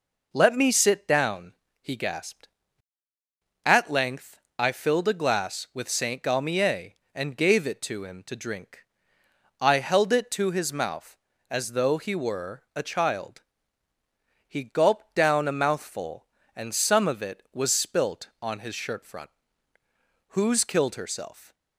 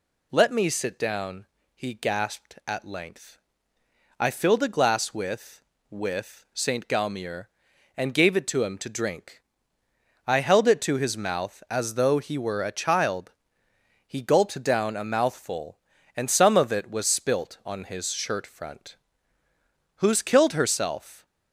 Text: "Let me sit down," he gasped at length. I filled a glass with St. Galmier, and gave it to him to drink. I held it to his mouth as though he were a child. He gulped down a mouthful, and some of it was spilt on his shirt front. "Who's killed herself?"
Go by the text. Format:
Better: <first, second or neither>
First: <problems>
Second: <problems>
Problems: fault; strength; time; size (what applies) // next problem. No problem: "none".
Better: first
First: none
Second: says "with" twice; at 5.8 s